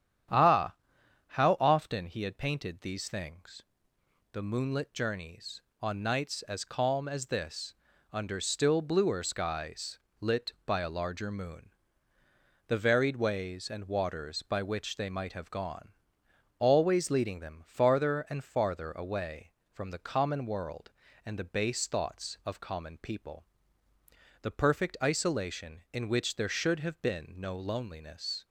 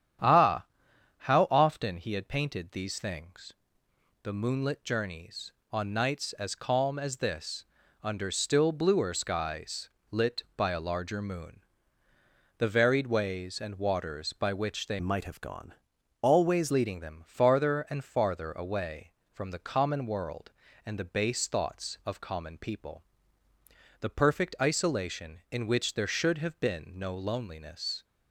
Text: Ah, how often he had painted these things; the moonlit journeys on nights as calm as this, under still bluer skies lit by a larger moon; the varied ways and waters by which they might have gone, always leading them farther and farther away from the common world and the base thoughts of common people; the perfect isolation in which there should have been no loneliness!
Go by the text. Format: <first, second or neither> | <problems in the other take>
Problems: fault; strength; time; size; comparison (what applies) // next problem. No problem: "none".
first | starts louder than the rest; strong; until 1.8 s; 9.5 dB; strong in the first // pauses between "skies" and "lit"; slight; at 9.8 s; 0.24 s long; slight in the first // changes voice from "might" to "always"; from 14.9 to 16.7 s; 1.8 s long